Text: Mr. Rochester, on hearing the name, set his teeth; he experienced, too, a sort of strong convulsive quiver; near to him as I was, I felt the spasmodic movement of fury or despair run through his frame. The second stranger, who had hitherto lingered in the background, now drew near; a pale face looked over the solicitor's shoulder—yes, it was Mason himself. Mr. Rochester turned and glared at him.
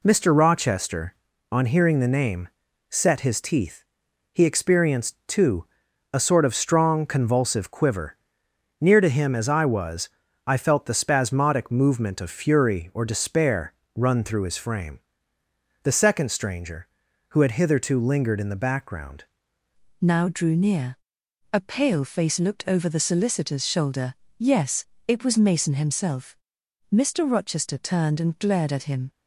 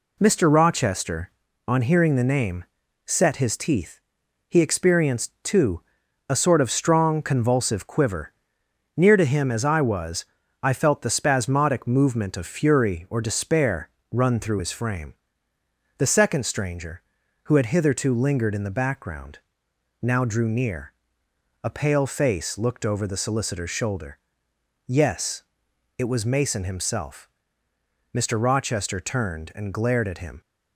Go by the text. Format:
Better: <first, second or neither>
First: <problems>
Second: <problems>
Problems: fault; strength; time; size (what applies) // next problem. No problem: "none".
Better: second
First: pauses between "despair" and "run"; slight; at 13.7 s; 0.20 s long // changes voice at "now"; from 19.9 s on; 9.1 s long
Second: pauses between "despair" and "run"; slight; at 13.8 s; 0.20 s long